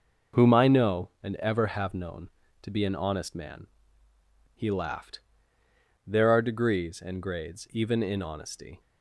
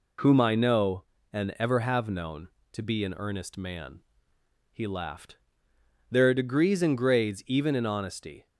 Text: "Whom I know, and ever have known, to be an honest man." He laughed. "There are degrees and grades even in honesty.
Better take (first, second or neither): first